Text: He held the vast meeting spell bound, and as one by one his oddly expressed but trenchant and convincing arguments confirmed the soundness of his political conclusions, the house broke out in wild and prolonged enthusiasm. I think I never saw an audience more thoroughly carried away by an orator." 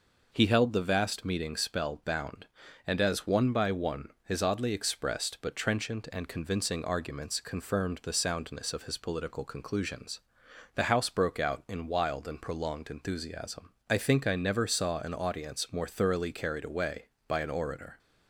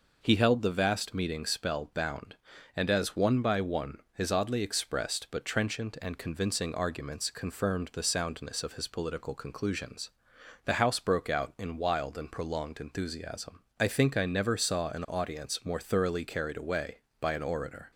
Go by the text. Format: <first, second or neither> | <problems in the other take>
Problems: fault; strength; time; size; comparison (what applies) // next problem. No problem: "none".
neither | pauses between "one" and "his"; slight; the same in both